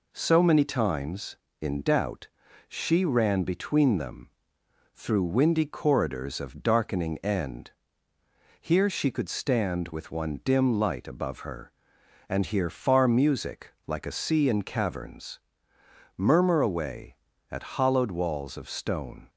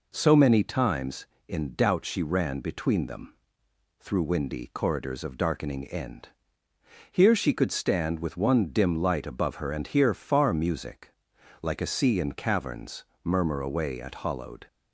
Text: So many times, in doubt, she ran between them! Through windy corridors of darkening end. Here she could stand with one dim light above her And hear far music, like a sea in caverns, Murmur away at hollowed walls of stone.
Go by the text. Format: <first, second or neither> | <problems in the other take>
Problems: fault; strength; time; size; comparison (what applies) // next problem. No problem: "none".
first | stops before "walls of stone"; at 14.6 s